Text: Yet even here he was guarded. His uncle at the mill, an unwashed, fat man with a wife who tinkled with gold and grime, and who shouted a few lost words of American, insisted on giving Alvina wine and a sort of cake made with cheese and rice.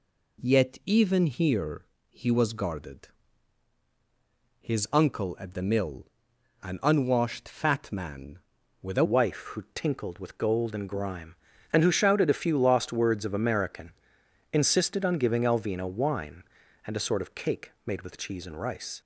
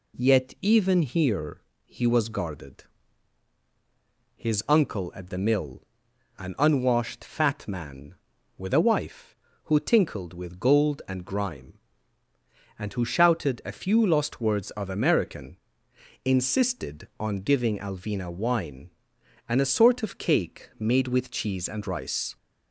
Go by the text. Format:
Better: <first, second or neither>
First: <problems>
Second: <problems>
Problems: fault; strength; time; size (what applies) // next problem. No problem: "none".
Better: second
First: pauses between "here" and "he"; slight; at 1.8 s; 0.24 s long // changes voice at "wife"; from 9.0 s on; 10.0 s long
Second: pauses between "here" and "he"; slight; at 1.6 s; 0.24 s long